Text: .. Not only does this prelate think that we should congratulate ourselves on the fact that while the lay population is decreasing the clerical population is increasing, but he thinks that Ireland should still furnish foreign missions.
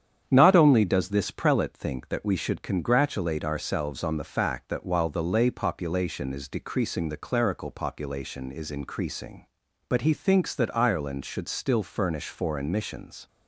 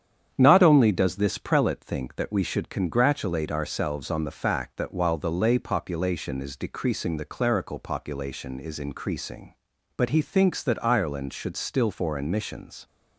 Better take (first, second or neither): first